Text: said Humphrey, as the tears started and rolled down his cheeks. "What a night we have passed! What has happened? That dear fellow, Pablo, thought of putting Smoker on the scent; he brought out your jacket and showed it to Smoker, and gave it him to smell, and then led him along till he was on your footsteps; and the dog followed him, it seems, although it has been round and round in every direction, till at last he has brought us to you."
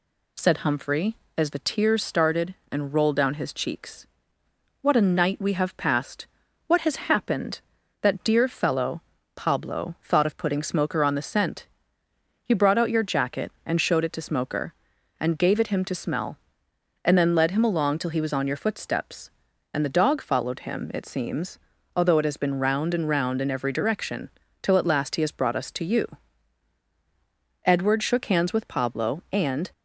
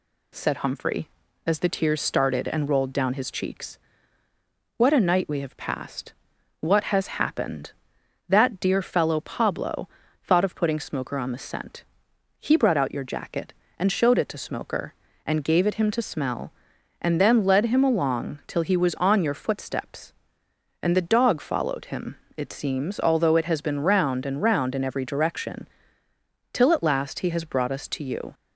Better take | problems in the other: second | goes on to say "Edward shook hands with Pablo and"; strong; from 27.6 s on; 2.0 s long

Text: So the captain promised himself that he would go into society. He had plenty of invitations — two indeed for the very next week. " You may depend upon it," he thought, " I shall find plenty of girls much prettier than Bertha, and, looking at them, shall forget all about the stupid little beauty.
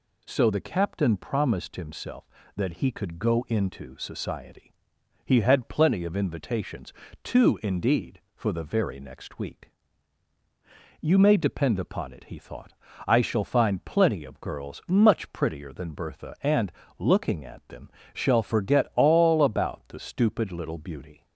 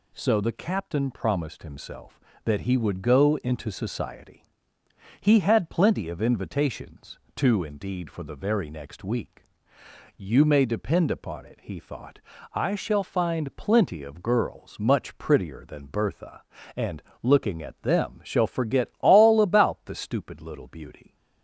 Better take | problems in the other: second | says "could" for "would"; at 2.9 s

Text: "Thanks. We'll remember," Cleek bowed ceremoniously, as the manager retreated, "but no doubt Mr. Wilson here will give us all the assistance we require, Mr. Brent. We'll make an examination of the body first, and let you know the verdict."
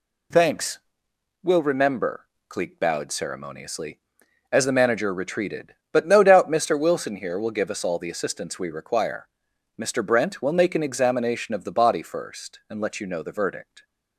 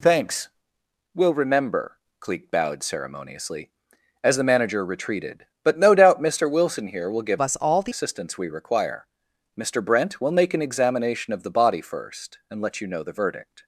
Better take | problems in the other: first | changes voice from "us" to "the"; from 7.3 to 7.9 s; 0.6 s long

